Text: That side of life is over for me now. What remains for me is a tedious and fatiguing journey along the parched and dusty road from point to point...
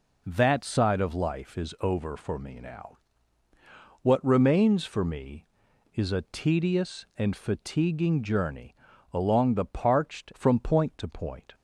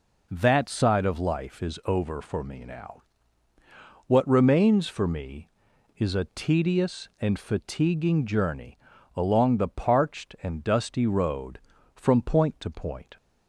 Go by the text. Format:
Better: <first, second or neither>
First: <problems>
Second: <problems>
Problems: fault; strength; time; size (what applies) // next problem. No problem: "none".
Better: second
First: pauses between "journey" and "along"; slight; at 8.7 s; 0.36 s long // skips "and dusty road"; at 10.3 s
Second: pauses between "journey" and "along"; slight; at 8.7 s; 0.36 s long